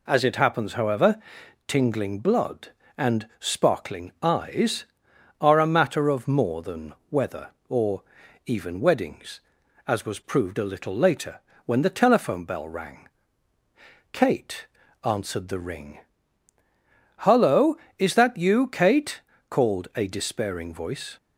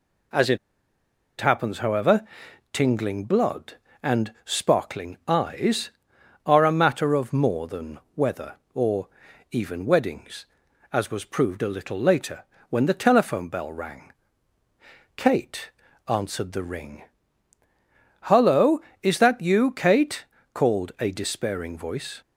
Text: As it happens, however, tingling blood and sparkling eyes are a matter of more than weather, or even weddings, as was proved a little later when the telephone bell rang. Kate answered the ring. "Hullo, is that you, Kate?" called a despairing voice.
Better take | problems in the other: first | pauses between "it" and "happens"; noticeable; at 0.5 s; 0.82 s long // pauses between "than" and "weather"; slight; at 7.9 s; 0.16 s long; slight in the first // pauses between "or" and "even"; at 9.0 s; 0.44 s long; also in the first // pauses between "later" and "when"; slight; at 12.4 s; 0.26 s long; slight in the first // pauses between "Kate" and "answered"; at 15.7 s; 0.38 s long; also in the first

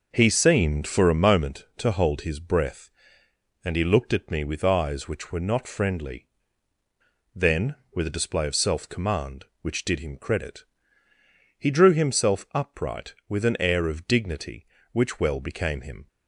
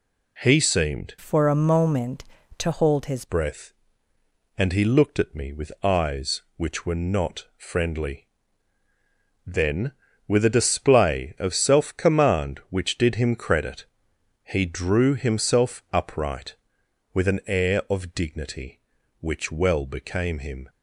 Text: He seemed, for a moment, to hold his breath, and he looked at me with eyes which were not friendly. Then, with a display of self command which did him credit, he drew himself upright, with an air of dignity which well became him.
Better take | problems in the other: first | changes voice from "for" to "his"; from 1.2 to 3.2 s; 2.0 s long

